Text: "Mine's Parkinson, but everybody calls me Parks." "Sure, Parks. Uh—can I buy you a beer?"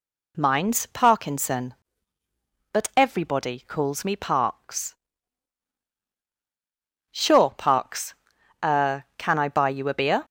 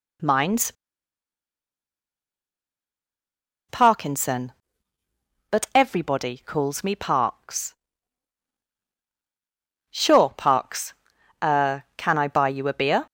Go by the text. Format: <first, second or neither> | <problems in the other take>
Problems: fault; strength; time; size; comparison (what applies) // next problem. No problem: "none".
first | pauses between "Mine's" and "Parkinson"; strong; at 0.7 s; 2.9 s long